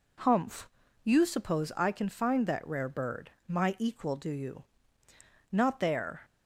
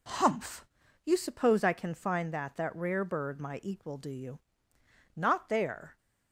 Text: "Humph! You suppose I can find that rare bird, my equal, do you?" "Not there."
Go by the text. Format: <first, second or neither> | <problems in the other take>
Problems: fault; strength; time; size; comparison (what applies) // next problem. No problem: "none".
first | says "that" twice; at 2.5 s